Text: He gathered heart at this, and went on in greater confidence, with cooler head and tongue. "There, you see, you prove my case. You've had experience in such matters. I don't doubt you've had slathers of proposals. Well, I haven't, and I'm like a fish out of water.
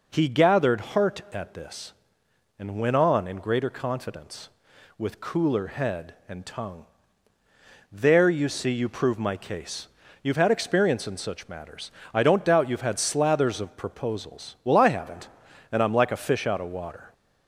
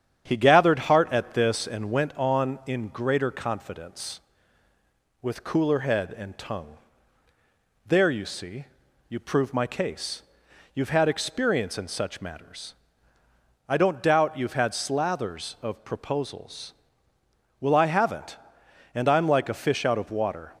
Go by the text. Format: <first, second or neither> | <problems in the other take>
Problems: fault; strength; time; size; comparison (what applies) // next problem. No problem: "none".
first | starts louder than the rest; strong; until 1.8 s; 8.5 dB